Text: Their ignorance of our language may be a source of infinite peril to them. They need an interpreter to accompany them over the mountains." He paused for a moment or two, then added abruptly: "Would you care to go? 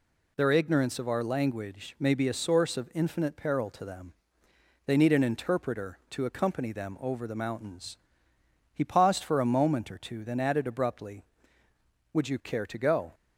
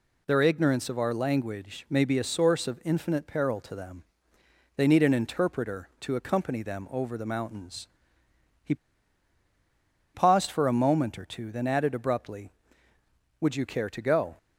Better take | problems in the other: first | pauses between "He" and "paused"; strong; at 8.7 s; 1.4 s long

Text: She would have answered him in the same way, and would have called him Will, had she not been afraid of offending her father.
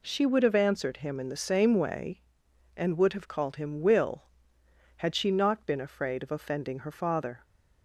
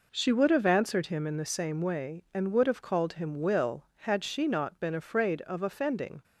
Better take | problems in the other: first | stops before "her father"; at 6.2 s

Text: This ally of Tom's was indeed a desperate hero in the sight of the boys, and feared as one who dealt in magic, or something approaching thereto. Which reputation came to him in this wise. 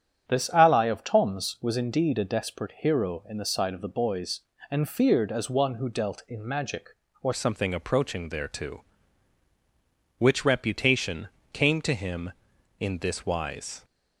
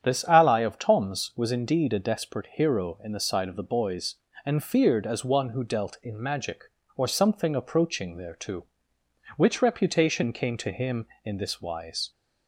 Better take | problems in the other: second | starts louder than the rest; strong; until 1.3 s; 8 dB; strong in the second // changes voice at "something"; from 7.3 s on; 6.5 s long // pauses between "reputation" and "came"; slight; at 11.2 s; 0.24 s long

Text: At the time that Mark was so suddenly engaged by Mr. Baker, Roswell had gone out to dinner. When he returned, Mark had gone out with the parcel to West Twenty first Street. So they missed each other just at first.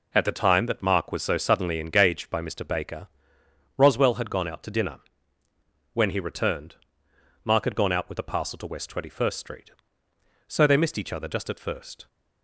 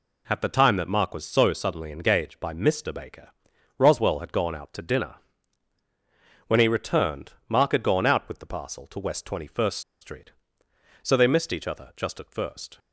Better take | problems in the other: first | pauses between "first" and "Street"; slight; at 9.8 s; 0.21 s long

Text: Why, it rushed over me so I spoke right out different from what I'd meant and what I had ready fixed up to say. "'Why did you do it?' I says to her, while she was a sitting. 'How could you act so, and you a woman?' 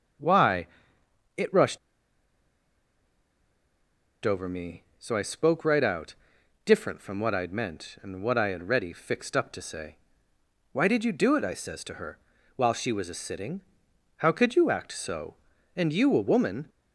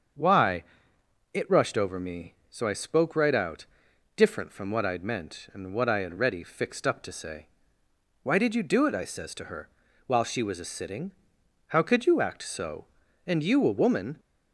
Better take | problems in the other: second | starts louder than the rest; until 4.3 s; 7 dB; also in the second // pauses between "rushed" and "over"; strong; at 1.7 s; 2.4 s long // pauses between "out" and "different"; noticeable; at 6.1 s; 0.50 s long; noticeable in the second

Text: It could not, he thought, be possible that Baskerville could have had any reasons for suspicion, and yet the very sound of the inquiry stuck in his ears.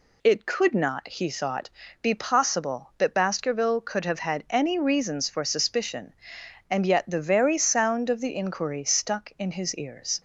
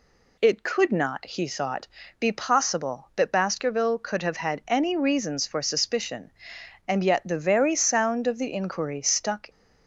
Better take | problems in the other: first | stops before "in his ears"; at 9.4 s

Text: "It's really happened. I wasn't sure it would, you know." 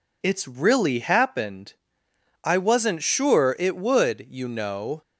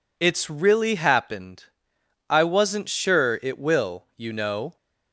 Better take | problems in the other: first | says "will" for "would"; at 3.5 s

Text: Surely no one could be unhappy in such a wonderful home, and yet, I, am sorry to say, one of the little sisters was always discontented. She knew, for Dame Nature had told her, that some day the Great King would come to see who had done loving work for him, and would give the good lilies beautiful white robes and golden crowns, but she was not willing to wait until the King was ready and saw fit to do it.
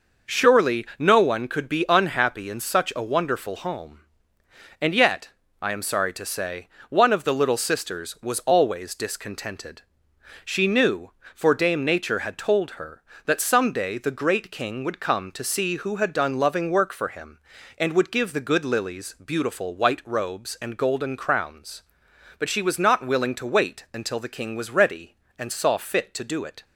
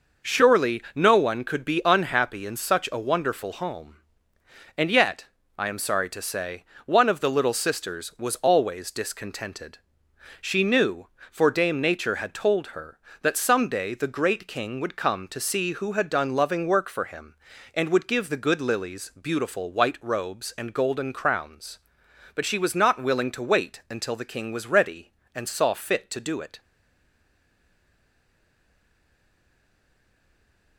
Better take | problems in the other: first | stays silent after the last word; strong; from 26.5 s on; 4.2 s long

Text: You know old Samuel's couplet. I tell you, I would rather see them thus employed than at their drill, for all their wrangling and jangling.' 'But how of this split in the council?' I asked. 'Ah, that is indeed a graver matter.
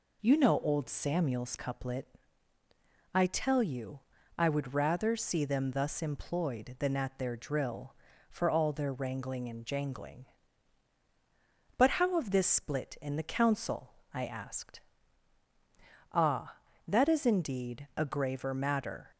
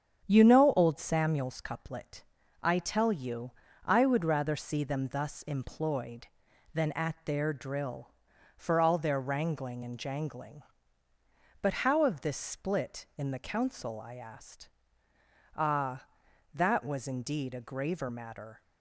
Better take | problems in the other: first | starts louder than the rest; strong; until 1.2 s; 8 dB // says "was" for "is"; at 16.8 s

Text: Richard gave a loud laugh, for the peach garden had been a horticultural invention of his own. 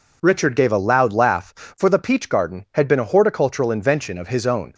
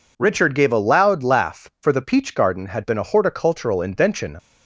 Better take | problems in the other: first | stops before "of his own"; at 4.3 s

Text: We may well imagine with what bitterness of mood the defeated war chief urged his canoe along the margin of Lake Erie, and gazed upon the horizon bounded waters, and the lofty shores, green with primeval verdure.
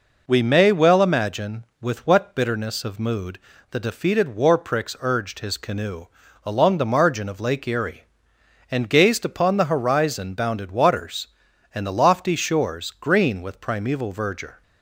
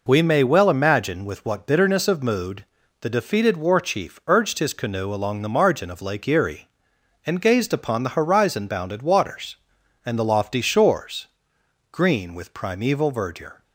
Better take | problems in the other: second | pauses between "mood" and "the"; slight; at 3.3 s; 0.32 s long; also in the second // says "pricks" for "chief"; at 4.5 s // pauses between "canoe" and "along"; at 6.0 s; 0.38 s long

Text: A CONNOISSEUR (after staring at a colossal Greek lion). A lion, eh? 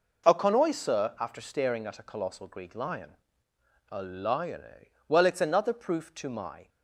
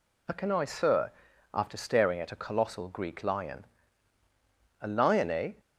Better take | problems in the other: second | goes on to say "Well it's another proof to my"; from 5.0 s on; 1.6 s long

